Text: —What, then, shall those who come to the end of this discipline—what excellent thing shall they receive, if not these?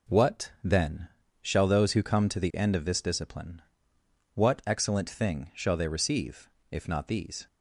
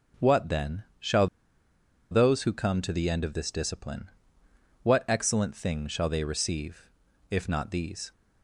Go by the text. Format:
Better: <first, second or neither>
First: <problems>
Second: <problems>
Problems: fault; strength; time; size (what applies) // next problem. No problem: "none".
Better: first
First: none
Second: pauses between "shall" and "those"; noticeable; at 1.2 s; 0.83 s long